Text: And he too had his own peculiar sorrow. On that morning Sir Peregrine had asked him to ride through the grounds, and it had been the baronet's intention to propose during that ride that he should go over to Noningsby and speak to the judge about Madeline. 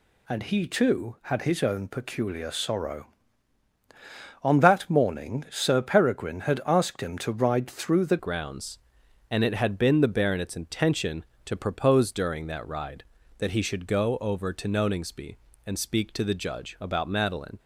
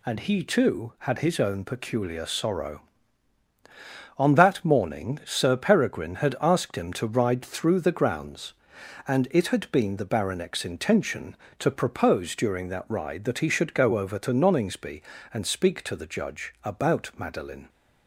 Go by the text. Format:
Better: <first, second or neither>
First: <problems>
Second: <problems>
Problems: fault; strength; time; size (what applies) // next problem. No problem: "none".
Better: second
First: changes voice at "grounds"; from 8.1 s on; 9.4 s long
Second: none